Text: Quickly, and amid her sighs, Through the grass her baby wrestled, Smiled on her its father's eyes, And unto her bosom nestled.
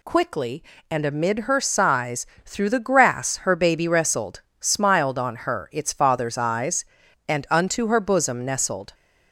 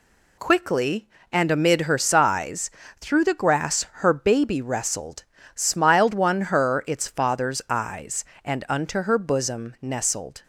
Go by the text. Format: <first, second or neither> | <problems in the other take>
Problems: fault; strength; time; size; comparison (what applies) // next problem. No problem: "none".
first | says "one" for "on"; at 6.1 s